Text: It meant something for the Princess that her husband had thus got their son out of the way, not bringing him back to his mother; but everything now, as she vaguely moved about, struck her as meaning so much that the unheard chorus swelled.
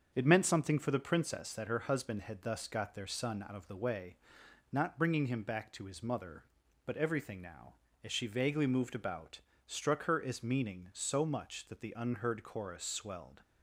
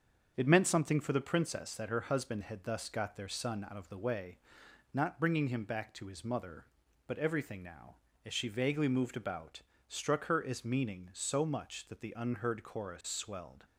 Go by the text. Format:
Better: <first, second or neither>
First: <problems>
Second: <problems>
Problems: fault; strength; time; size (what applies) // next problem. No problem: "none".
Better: neither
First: starts louder than the rest; until 1.1 s; 7 dB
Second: starts louder than the rest; until 1.3 s; 7 dB